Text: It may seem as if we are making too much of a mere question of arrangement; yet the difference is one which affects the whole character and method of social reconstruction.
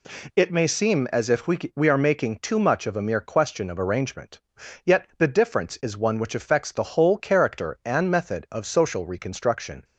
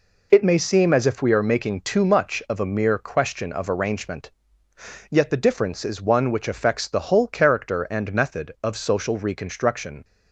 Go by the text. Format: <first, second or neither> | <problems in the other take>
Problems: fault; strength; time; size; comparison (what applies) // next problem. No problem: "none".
second | says "we" twice; at 1.7 s